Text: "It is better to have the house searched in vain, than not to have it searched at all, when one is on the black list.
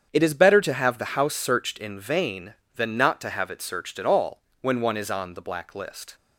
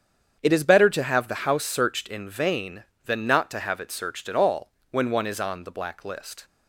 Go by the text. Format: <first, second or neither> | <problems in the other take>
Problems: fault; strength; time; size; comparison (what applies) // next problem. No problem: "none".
neither | starts louder than the rest; strong; the same in both